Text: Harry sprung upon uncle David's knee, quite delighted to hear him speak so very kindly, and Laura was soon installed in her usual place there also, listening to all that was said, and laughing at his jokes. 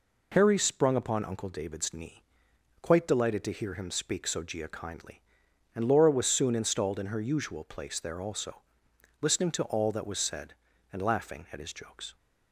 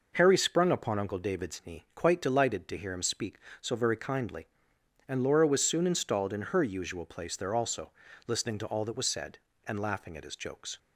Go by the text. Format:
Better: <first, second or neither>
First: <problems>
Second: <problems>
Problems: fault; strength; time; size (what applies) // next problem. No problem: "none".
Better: second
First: says "gia" for "very"; at 4.4 s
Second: none